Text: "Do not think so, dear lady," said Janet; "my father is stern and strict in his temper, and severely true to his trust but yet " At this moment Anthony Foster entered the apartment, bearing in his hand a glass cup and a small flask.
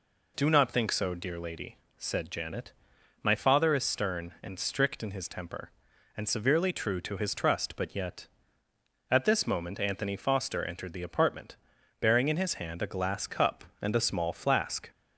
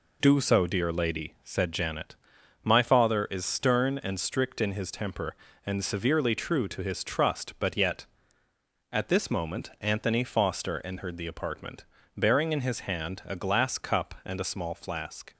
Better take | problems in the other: first | skips "not think"; at 0.3 s

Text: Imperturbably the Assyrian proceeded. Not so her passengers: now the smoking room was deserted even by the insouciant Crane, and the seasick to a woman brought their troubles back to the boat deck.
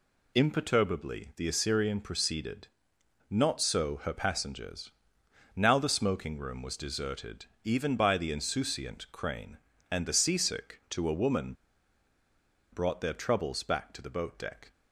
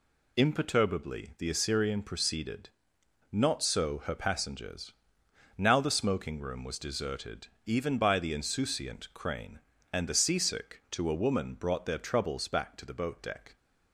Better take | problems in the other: second | pauses between "deserted" and "even"; slight; at 7.4 s; 0.18 s long; slight in the second // pauses between "woman" and "brought"; at 11.5 s; 1.1 s long

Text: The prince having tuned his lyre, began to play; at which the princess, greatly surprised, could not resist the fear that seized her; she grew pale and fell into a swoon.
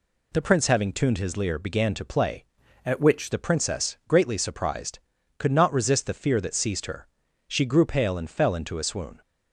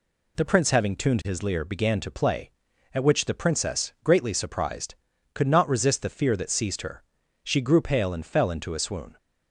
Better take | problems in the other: second | changes voice from "at" to "which"; from 2.8 to 3.3 s; 0.5 s long

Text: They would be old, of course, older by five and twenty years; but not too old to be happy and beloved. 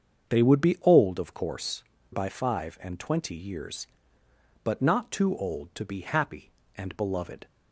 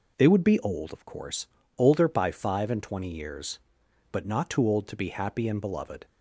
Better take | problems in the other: second | starts louder than the rest; until 1.3 s; 7 dB // skips "older"; at 1.9 s

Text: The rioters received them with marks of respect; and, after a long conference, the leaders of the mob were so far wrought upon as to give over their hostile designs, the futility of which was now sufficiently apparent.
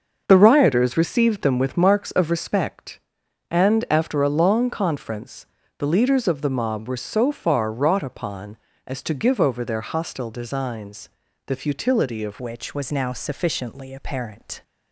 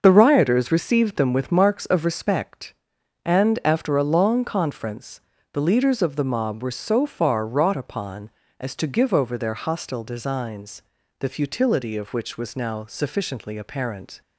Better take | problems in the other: second | starts louder than the rest; until 1.2 s; 6 dB; also in the second // changes voice at "which"; from 12.4 s on; 2.2 s long

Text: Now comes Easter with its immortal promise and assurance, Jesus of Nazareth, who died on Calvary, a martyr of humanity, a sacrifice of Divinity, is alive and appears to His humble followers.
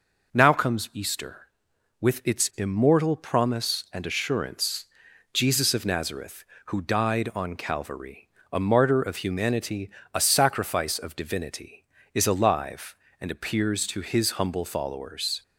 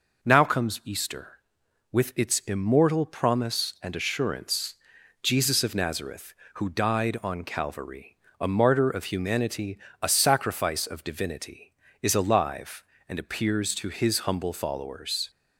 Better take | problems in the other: neither | none

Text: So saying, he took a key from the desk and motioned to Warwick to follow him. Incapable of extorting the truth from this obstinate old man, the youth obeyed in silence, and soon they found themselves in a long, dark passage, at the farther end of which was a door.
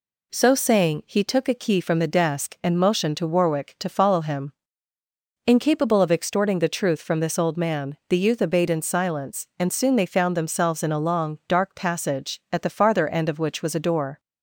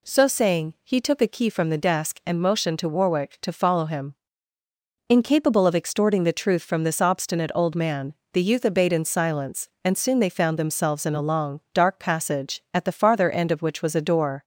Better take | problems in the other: second | skips "obstinate"; at 7.3 s

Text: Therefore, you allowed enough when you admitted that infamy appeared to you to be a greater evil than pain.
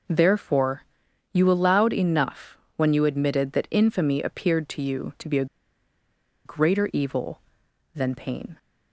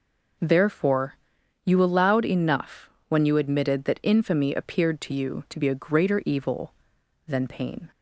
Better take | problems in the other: second | pauses between "enough" and "when"; slight; at 2.5 s; 0.18 s long; slight in the second // pauses between "a" and "greater"; at 5.4 s; 0.99 s long

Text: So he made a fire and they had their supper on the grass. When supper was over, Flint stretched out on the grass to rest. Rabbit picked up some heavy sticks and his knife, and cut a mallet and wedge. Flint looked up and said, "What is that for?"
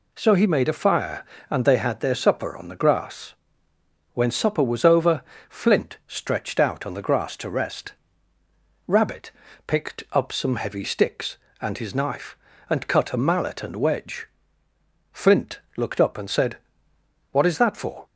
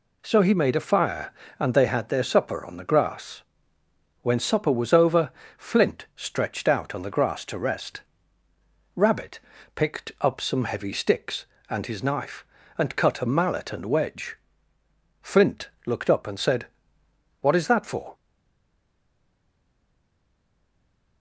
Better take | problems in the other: first | pauses between "Rabbit" and "picked"; slight; at 9.3 s; 0.36 s long; slight in the first // pauses between "Flint" and "looked"; slight; at 15.6 s; 0.16 s long; slight in the first // stays silent after the last word; strong; from 18.1 s on; 3.1 s long

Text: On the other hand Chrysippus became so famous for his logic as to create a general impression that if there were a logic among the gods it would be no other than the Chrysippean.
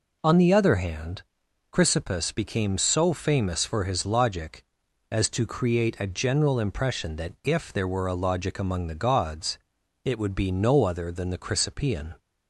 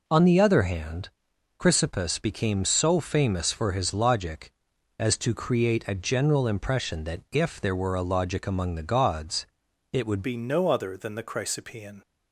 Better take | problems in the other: first | pauses between "hand" and "Chrysippus"; noticeable; at 1.0 s; 0.48 s long; noticeable in the first // pauses between "gods" and "it"; at 9.4 s; 0.44 s long; also in the first // changes voice at "be"; from 10.2 s on; 1.8 s long

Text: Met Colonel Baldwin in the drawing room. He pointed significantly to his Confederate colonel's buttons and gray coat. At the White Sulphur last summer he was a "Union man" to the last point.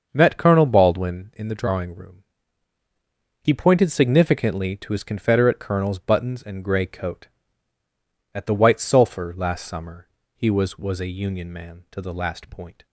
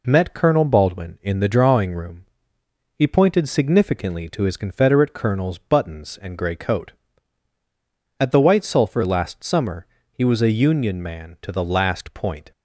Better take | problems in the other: second | starts louder than the rest; until 1.1 s; 6.5 dB // pauses between "summer" and "he"; slight; at 10.0 s; 0.28 s long; slight in the second // says "was" twice; at 10.7 s

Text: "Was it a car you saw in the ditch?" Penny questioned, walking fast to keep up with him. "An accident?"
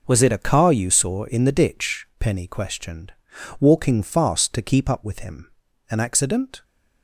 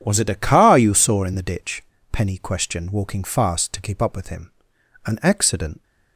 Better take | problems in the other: neither | none

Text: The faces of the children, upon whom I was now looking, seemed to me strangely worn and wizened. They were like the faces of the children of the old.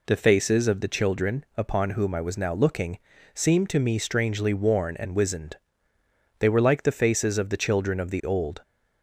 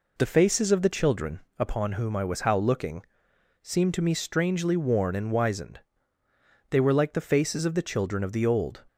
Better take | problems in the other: first | says "how" for "now"; at 2.4 s

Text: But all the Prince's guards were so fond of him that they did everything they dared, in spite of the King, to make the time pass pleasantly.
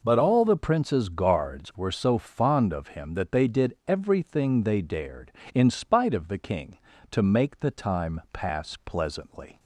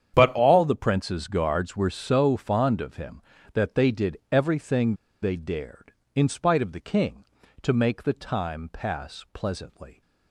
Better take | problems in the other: first | starts louder than the rest; strong; until 1.1 s; 8.5 dB // pauses between "everything" and "they"; slight; at 4.9 s; 0.27 s long

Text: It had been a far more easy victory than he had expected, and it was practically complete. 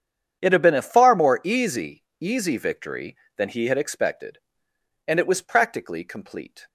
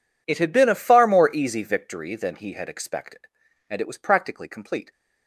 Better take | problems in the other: second | starts louder than the rest; strong; until 1.4 s; 8 dB // says "easy" twice; at 2.1 s

